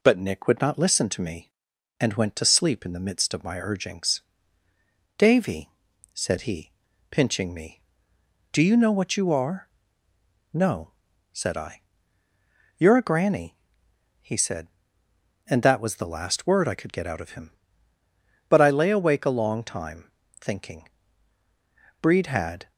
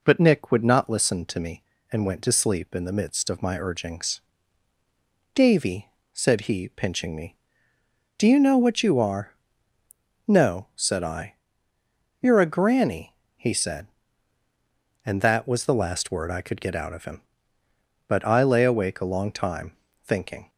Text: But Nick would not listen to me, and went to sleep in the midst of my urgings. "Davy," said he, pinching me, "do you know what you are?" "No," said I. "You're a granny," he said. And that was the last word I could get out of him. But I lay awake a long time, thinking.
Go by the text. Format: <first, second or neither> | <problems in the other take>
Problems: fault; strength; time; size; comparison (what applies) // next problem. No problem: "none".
second | goes on to say "Breed had"; noticeable; from 22.0 s on; 0.70 s long